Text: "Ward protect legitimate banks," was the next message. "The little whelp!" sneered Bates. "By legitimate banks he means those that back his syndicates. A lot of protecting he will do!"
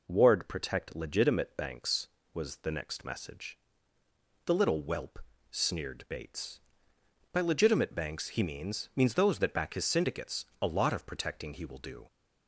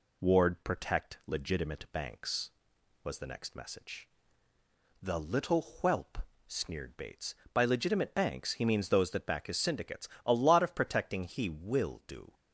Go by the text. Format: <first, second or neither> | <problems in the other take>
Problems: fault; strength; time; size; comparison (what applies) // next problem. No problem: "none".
second | says "means" twice; at 8.9 s